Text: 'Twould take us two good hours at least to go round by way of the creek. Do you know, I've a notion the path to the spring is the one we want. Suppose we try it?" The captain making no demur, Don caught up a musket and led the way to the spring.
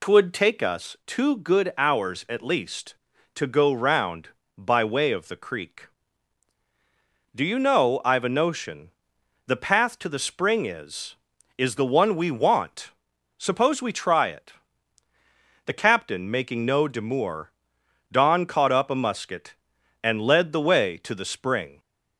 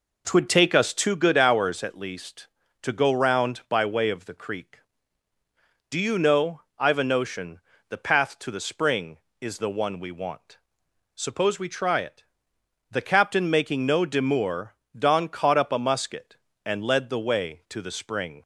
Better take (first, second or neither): second